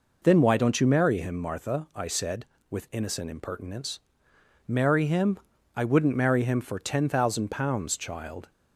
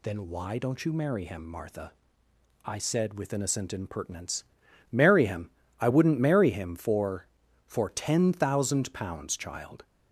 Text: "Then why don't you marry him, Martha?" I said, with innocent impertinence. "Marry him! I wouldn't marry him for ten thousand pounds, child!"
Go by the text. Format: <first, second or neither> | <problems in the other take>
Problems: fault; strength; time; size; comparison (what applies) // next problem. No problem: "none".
first | says "for" twice; at 7.6 s